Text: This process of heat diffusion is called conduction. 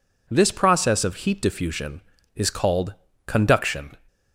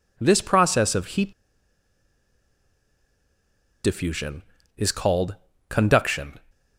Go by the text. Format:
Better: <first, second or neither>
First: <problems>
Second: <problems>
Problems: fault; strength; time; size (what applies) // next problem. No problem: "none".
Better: first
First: pauses between "called" and "conduction"; slight; at 2.9 s; 0.32 s long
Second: pauses between "heat" and "diffusion"; strong; at 1.3 s; 2.5 s long // pauses between "called" and "conduction"; slight; at 5.3 s; 0.34 s long